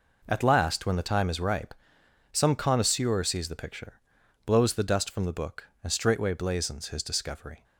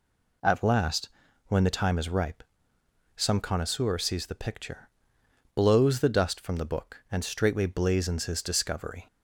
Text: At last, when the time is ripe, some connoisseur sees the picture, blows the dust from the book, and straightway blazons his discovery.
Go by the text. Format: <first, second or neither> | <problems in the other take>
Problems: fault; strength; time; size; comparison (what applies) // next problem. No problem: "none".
neither | none